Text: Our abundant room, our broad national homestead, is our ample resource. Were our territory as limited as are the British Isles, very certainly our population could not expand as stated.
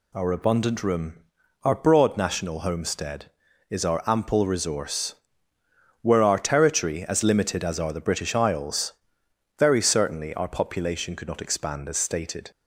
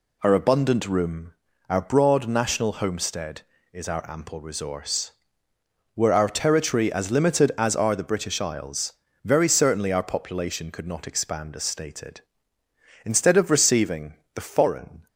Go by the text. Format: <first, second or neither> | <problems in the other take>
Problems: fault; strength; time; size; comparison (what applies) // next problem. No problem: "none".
first | goes on to say "Instead of receiving the foreign"; strong; from 13.0 s on; 2.0 s long